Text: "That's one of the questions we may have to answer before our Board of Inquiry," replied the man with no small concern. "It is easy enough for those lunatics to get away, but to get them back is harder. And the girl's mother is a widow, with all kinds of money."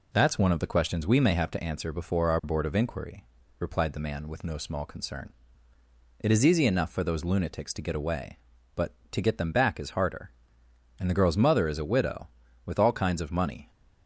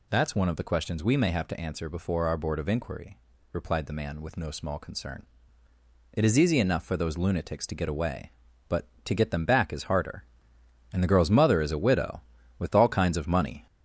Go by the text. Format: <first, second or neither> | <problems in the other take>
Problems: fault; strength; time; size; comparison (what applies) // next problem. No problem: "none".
first | gets louder; noticeable; throughout; 4 dB